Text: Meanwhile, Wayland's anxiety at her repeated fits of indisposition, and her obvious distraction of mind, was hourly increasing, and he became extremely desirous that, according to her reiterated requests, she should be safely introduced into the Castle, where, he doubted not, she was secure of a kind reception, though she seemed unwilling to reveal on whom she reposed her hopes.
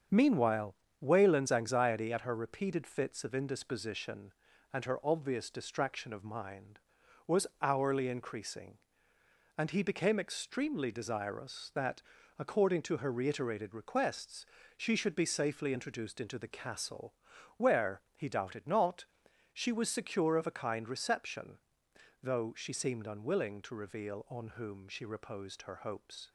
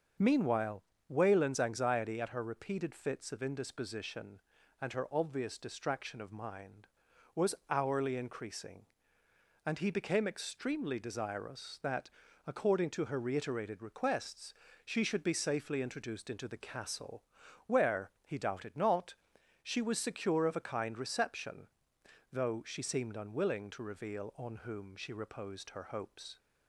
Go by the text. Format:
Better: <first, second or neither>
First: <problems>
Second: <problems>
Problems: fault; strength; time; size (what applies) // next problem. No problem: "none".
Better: second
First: gets quieter; noticeable; throughout; 5.5 dB // starts louder than the rest; until 1.3 s; 7 dB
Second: starts louder than the rest; until 1.4 s; 6.5 dB